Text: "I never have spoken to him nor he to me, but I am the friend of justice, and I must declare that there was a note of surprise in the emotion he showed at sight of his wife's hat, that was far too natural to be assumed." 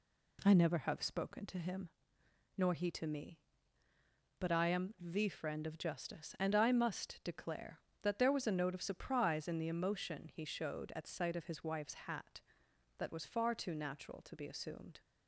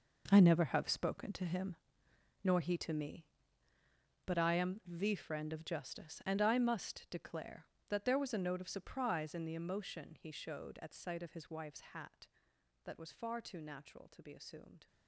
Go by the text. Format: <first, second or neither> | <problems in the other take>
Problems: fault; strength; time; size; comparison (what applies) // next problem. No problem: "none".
first | gets quieter; strong; throughout; 13 dB // pauses between "him" and "nor"; noticeable; at 1.7 s; 0.66 s long; noticeable in the first